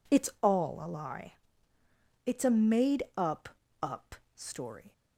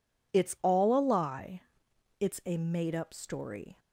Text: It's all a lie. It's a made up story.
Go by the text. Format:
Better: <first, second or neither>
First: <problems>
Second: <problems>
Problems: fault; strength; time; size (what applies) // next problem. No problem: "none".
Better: second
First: says "up" twice; at 3.8 s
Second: none